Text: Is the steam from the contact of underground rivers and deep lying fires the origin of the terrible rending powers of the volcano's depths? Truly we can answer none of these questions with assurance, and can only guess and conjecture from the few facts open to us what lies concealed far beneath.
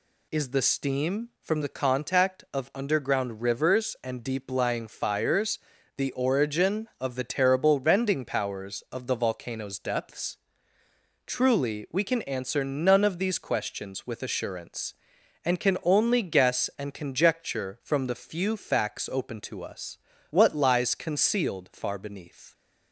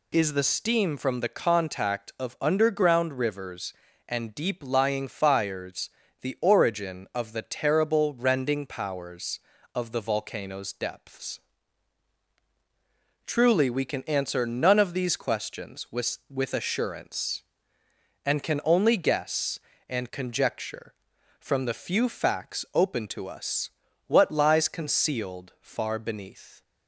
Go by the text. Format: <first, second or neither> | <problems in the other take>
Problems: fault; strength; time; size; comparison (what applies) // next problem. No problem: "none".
first | pauses between "fires" and "the"; slight; at 5.8 s; 0.32 s long; also in the first // says "with" twice; at 16.2 s // pauses between "us" and "what"; at 23.6 s; 0.40 s long; slight in the first